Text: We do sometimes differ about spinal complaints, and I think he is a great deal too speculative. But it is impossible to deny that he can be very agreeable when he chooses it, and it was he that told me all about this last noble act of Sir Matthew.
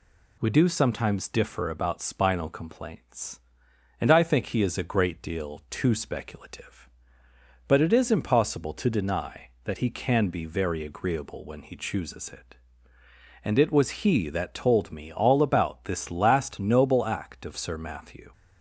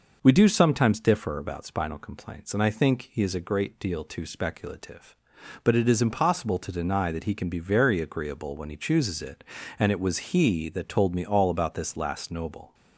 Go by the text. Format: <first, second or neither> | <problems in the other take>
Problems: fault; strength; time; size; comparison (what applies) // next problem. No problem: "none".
first | stops before "act of Sir Matthew"; at 12.7 s